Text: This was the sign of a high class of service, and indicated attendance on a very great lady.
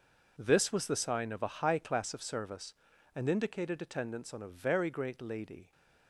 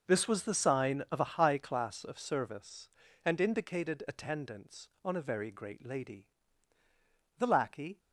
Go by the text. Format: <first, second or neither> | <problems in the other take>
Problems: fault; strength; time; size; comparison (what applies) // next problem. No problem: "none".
first | goes on to say "The lackey"; from 7.3 s on; 0.60 s long